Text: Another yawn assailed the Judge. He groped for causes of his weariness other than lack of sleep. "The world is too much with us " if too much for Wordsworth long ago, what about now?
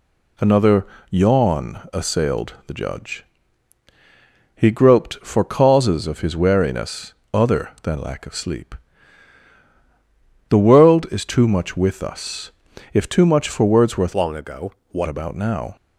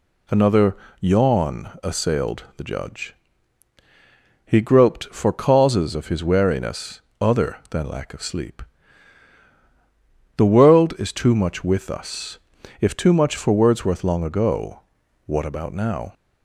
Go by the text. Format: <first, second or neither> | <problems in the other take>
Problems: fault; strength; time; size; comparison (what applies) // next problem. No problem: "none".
second | pauses between "Another" and "yawn"; slight; at 0.8 s; 0.24 s long; slight in the second // pauses between "weariness" and "other"; slight; at 7.1 s; 0.18 s long; slight in the second // changes voice from "long" to "what"; from 14.1 to 15.0 s; 0.9 s long